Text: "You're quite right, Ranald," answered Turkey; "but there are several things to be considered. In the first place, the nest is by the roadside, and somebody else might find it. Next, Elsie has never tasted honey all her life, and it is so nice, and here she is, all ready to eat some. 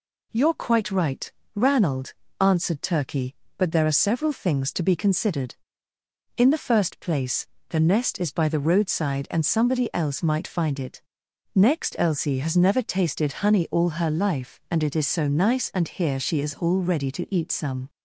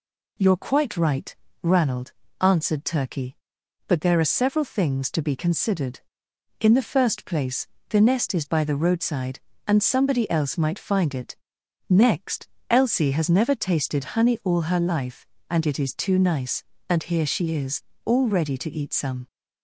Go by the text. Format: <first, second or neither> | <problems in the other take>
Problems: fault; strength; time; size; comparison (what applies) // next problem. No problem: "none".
first | says "too" for "so"; at 15.9 s